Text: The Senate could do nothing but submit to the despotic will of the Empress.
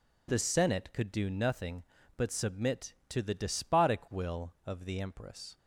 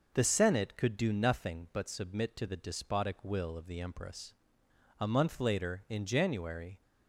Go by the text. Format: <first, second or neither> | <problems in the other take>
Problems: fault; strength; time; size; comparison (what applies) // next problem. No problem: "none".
first | goes on to say "A month later in January"; strong; from 4.9 s on; 1.8 s long